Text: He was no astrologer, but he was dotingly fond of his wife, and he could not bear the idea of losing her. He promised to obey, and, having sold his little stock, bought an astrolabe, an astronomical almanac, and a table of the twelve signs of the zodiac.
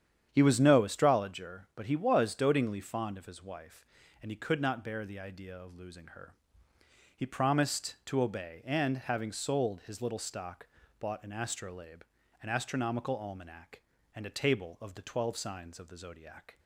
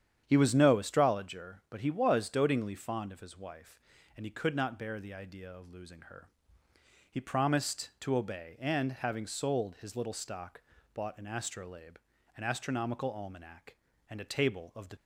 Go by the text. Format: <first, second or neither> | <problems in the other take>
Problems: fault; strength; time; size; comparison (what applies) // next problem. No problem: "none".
first | starts louder than the rest; strong; until 1.2 s; 9 dB; strong in the first // stops before "twelve signs of the zodiac"; at 14.9 s